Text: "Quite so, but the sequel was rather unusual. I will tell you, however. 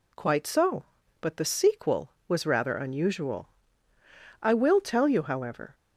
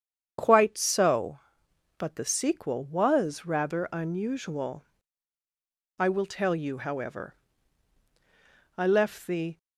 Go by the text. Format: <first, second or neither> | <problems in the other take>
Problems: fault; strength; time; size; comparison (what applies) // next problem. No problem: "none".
first | starts louder than the rest; strong; until 2.0 s; 8 dB // goes on to say "I left the"; noticeable; from 8.7 s on; 0.80 s long